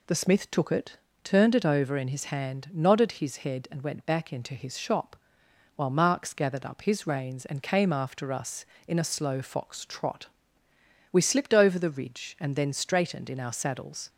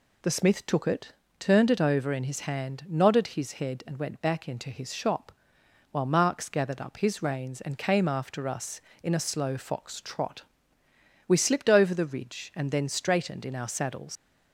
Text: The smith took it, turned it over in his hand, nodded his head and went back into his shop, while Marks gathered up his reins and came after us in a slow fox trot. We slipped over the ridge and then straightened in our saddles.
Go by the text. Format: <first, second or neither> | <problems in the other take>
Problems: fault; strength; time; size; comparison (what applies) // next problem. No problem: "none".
first | leaves "saddles" unfinished; at 14.1 s; 90 ms